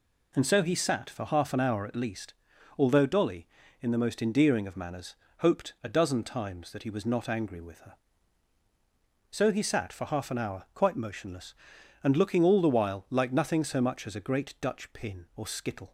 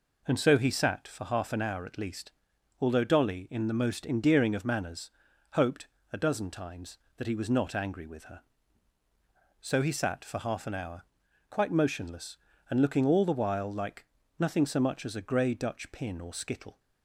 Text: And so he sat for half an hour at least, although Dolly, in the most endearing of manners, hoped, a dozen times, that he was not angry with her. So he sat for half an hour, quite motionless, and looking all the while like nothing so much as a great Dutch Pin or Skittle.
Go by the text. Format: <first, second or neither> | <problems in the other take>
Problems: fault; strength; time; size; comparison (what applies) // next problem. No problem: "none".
first | pauses between "like" and "nothing"; slight; at 14.0 s; 0.34 s long // says "grey" for "great"; at 15.2 s